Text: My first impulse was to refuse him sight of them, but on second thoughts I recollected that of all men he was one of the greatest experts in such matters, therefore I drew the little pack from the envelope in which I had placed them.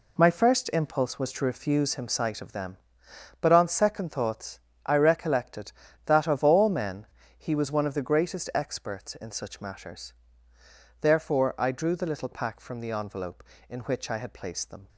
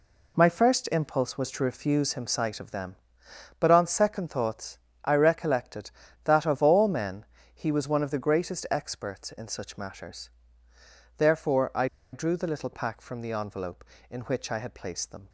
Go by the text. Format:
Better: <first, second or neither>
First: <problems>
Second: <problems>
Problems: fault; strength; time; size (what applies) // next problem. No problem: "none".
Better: first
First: pauses between "thoughts" and "I"; slight; at 4.5 s; 0.26 s long // pauses between "men" and "he"; slight; at 7.0 s; 0.32 s long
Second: pauses between "thoughts" and "I"; slight; at 4.7 s; 0.26 s long // pauses between "men" and "he"; slight; at 7.2 s; 0.30 s long // pauses between "I" and "drew"; slight; at 11.8 s; 0.26 s long